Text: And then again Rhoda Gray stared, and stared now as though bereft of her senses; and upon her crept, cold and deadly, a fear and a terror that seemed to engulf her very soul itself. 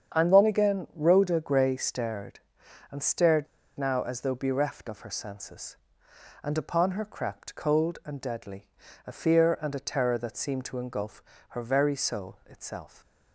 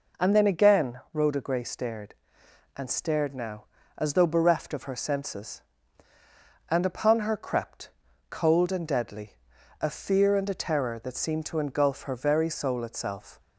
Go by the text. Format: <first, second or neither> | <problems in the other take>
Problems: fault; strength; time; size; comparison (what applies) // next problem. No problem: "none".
second | starts louder than the rest; strong; until 1.2 s; 7.5 dB // pauses between "stared" and "now"; slight; at 3.4 s; 0.31 s long // pauses between "engulf" and "her"; slight; at 11.2 s; 0.28 s long